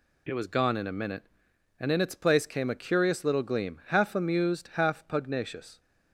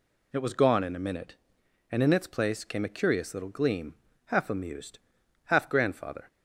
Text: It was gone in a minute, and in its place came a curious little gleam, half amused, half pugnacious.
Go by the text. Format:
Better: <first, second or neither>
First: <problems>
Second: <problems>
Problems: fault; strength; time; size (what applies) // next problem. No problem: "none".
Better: first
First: none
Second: says "grandfather" for "pugnacious"; at 5.6 s